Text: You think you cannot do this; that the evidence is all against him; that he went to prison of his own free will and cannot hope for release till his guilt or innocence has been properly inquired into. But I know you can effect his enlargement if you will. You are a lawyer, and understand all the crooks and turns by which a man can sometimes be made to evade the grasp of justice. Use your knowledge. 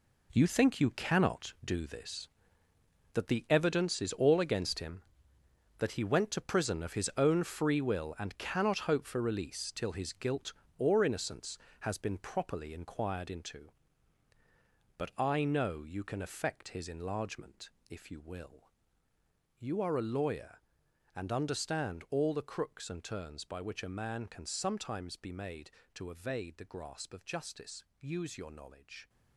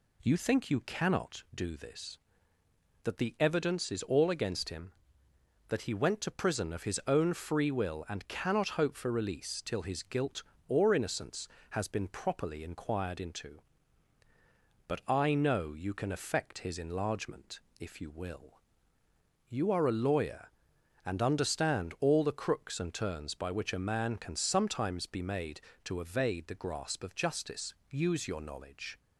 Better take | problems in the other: second | gets quieter; strong; throughout; 11 dB // pauses between "enlargement" and "if"; slight; at 17.6 s; 0.20 s long; slight in the second

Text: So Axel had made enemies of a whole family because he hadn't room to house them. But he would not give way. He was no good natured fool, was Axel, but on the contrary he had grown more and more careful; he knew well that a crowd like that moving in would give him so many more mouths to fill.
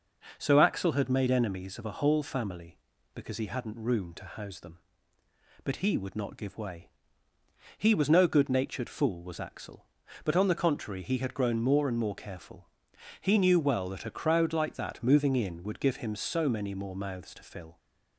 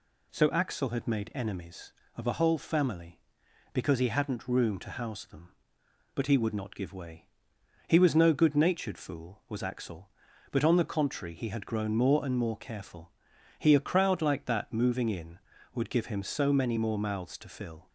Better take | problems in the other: first | skips "knew well that"; at 13.7 s

